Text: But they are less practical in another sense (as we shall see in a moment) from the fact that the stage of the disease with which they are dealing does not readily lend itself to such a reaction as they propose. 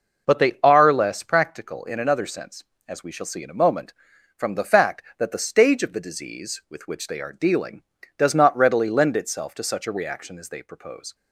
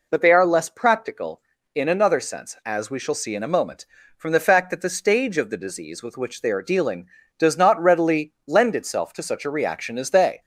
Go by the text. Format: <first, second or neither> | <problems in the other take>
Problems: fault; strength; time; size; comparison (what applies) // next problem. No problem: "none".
first | stops before "propose"; at 10.4 s